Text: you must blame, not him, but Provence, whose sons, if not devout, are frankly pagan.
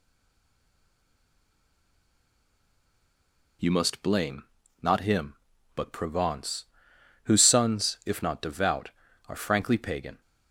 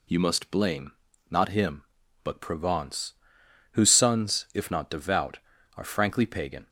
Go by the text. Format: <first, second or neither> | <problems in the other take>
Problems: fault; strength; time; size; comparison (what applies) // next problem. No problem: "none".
second | stays silent before the first word; strong; until 3.6 s; 3.6 s long